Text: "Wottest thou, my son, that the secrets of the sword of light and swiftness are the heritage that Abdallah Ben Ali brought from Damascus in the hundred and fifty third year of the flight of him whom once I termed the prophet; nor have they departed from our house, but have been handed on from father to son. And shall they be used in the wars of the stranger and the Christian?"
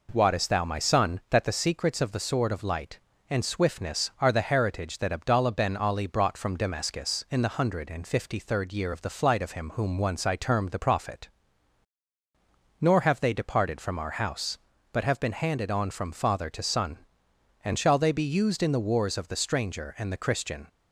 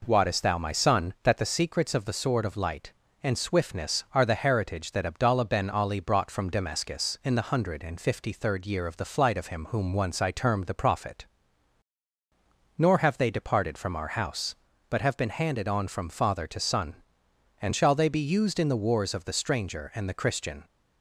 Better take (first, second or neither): neither